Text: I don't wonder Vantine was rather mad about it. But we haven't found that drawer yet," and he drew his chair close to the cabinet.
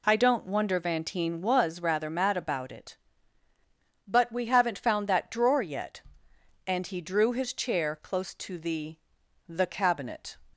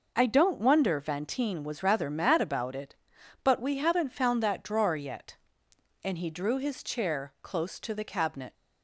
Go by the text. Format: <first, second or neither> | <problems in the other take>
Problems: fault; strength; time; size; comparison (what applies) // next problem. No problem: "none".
second | says "the" twice; at 9.4 s